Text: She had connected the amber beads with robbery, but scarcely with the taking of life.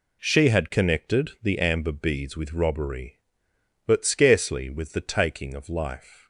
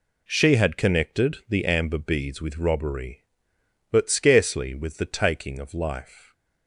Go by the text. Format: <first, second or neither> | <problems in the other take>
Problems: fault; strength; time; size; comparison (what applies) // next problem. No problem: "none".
neither | none